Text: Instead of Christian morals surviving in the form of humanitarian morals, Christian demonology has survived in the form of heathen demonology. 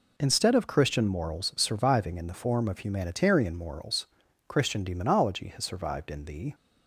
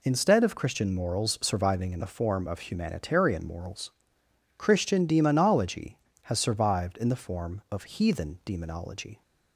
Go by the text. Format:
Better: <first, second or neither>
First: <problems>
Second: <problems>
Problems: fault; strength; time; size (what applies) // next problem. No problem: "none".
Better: second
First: stops before "form of heathen demonology"; at 6.5 s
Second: none